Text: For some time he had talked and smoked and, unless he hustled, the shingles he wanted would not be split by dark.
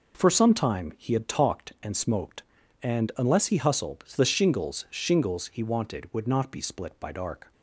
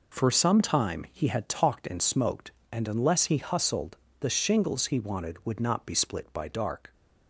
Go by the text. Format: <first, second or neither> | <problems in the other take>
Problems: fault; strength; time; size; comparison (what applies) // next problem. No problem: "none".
second | says "shingles" twice; at 4.8 s